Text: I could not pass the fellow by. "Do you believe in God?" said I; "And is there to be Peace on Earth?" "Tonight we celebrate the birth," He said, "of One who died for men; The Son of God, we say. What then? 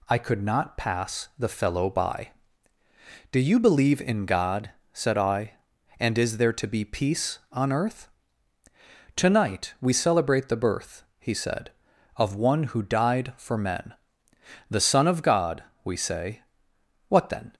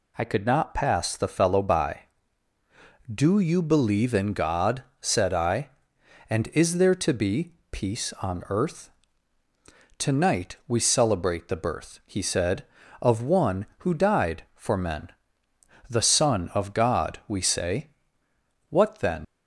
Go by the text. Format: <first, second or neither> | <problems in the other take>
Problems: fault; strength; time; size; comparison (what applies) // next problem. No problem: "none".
first | pauses between "be" and "Peace"; slight; at 7.5 s; 0.18 s long // leaves "then" unfinished; at 19.2 s; 80 ms